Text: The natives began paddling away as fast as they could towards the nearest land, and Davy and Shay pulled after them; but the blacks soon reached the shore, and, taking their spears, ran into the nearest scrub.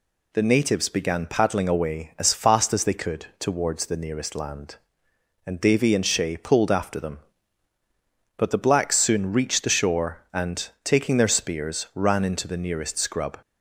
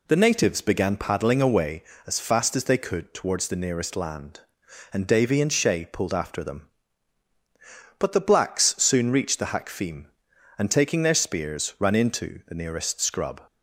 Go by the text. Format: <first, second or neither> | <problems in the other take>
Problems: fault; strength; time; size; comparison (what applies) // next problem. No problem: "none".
first | says "hakfim" for "shore"; at 9.5 s